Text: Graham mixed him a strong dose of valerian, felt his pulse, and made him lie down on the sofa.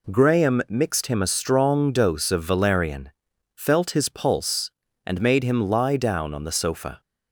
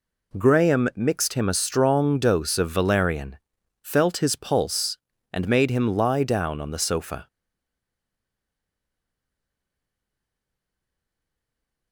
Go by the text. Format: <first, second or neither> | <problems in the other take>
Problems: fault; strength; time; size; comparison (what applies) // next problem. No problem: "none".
first | stays silent after the last word; strong; from 7.2 s on; 4.7 s long